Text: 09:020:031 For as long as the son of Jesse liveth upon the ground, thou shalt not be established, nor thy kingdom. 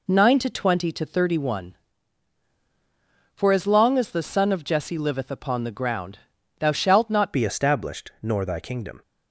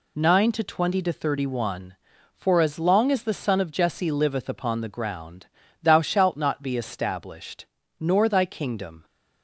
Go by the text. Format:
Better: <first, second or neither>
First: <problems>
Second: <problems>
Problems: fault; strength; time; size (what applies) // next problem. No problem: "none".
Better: second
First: changes voice at "be"; from 7.3 s on; 1.7 s long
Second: none